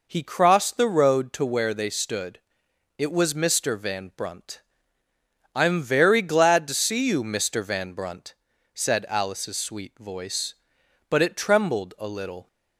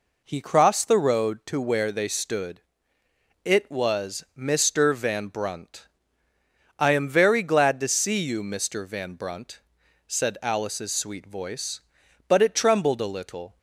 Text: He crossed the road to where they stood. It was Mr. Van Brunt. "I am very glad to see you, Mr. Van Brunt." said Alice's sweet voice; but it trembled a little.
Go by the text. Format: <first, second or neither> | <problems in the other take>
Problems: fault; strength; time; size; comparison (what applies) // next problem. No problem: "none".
neither | none